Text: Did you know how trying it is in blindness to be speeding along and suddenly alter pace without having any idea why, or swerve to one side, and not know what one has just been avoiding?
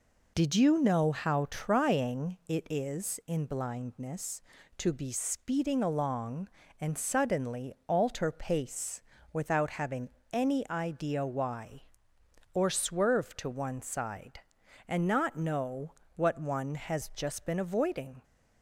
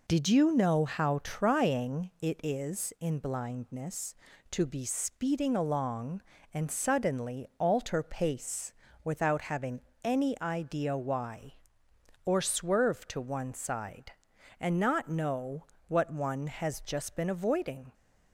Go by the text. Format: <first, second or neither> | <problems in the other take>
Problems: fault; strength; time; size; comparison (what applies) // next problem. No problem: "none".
neither | pauses between "pace" and "without"; slight; the same in both // pauses between "having" and "any"; slight; the same in both // pauses between "know" and "what"; slight; the same in both